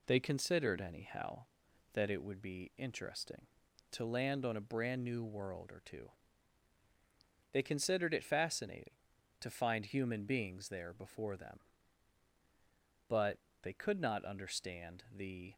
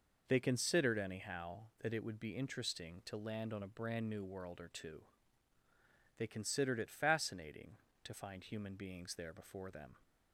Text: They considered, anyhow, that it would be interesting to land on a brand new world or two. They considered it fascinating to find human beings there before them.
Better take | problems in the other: second | goes on to say "But they could not understand the"; strong; from 13.0 s on; 2.4 s long

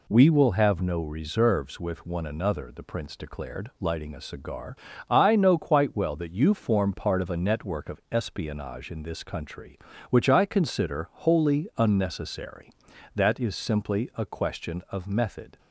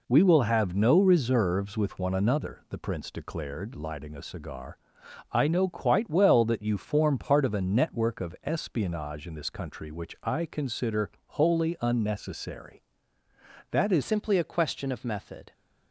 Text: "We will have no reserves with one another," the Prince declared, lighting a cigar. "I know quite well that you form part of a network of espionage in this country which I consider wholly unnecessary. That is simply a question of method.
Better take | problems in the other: first | pauses between "consider" and "wholly"; slight; at 11.0 s; 0.16 s long // changes voice at "simply"; from 14.0 s on; 1.5 s long

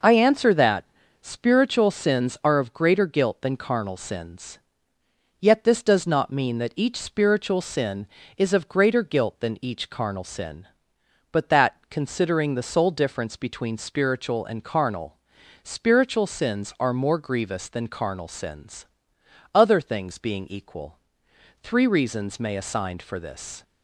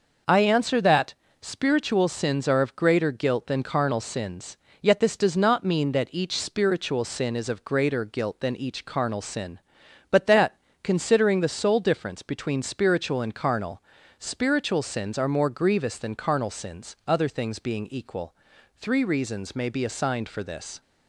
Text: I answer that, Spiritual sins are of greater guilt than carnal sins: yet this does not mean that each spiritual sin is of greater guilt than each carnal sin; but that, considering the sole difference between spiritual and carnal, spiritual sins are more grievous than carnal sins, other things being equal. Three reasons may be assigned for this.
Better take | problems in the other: second | skips "be"; at 22.5 s

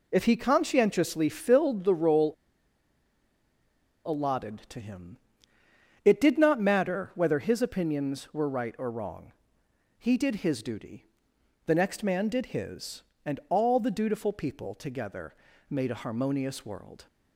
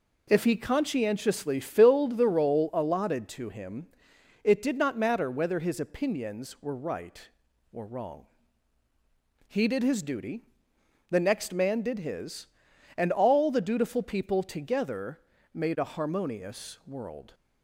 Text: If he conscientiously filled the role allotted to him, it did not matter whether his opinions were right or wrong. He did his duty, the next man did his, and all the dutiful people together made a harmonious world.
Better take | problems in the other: second | pauses between "role" and "allotted"; strong; at 2.3 s; 1.7 s long // pauses between "together" and "made"; slight; at 15.3 s; 0.34 s long; slight in the second

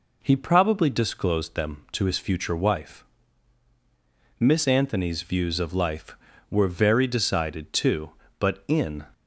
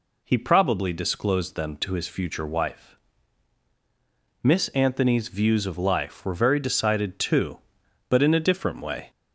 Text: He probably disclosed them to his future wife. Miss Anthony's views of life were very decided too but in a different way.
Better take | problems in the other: second | stops before "a different way"; at 9.1 s

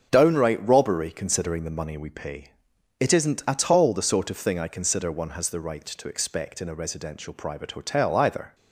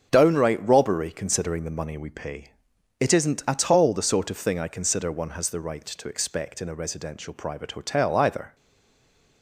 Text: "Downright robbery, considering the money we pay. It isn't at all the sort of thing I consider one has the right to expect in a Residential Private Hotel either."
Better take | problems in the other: first | starts louder than the rest; until 1.1 s; 6.5 dB; also in the first // stays silent after the last word; slight; from 8.5 s on; 0.9 s long

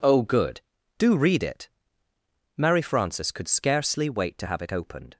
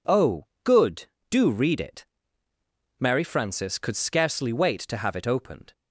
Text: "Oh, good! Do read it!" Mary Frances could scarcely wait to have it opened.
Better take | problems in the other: neither | none

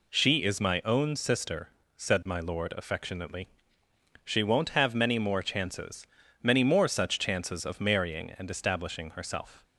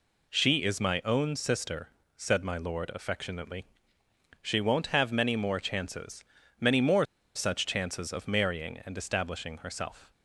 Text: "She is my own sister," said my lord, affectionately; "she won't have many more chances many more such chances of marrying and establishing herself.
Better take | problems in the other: first | pauses between "chances" and "many"; at 6.2 s; 0.38 s long; also in the first // pauses between "more" and "such"; slight; at 7.0 s; 0.30 s long

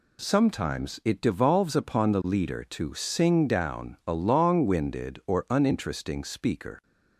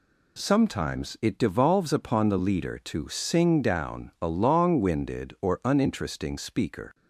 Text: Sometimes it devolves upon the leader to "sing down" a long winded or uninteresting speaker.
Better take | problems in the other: neither | none

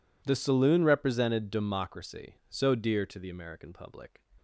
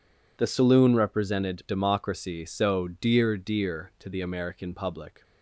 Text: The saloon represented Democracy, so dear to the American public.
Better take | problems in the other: first | says "dear" twice; at 3.3 s

